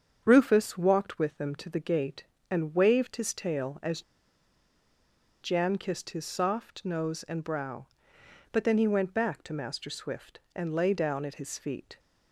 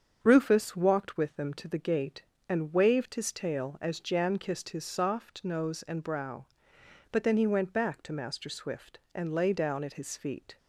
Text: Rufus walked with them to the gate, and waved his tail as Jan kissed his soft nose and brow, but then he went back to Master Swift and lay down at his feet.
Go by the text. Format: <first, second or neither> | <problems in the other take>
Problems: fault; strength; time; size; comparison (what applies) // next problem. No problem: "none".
second | starts louder than the rest; strong; until 1.2 s; 7.5 dB; strong in the second // pauses between "as" and "Jan"; strong; at 4.0 s; 1.4 s long